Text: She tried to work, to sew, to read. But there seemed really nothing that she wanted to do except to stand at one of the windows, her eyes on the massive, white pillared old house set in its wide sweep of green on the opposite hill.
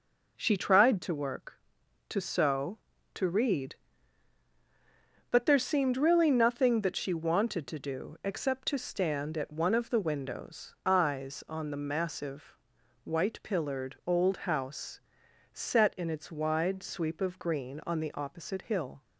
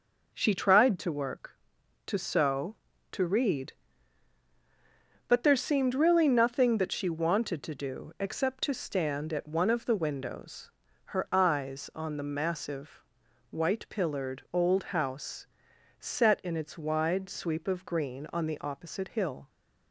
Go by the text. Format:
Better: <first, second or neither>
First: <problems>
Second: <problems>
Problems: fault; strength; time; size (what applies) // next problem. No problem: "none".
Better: second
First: skips "her"; at 10.8 s // pauses between "house" and "set"; noticeable; at 15.0 s; 0.52 s long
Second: pauses between "house" and "set"; noticeable; at 15.4 s; 0.52 s long